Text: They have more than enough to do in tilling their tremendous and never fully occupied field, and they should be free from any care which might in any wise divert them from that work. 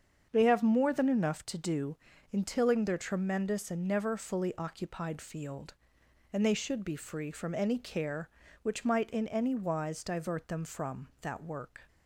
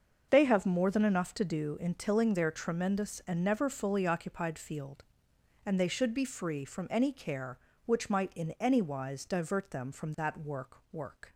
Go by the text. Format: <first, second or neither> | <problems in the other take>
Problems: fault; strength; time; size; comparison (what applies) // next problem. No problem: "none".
first | starts louder than the rest; until 1.3 s; 6.5 dB; strong in the first // says "work" twice; at 10.9 s